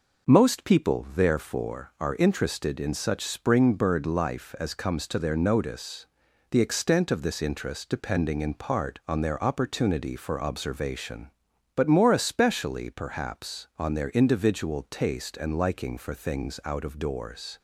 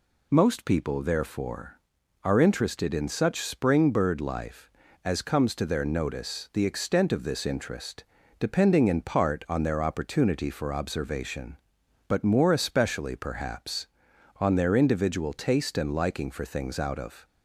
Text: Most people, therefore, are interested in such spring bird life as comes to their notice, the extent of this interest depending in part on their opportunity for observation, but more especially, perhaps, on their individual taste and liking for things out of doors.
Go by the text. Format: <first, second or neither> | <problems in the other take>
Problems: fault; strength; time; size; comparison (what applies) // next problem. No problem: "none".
first | pauses between "interest" and "depending"; slight; at 8.0 s; 0.36 s long // stops before "doors"; at 17.2 s